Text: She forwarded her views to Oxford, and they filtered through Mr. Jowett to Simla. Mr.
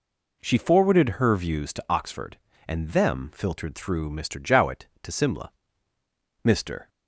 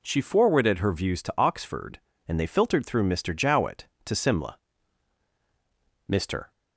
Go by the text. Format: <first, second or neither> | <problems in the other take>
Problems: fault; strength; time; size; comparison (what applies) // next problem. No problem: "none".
second | says "them" for "they"; at 2.9 s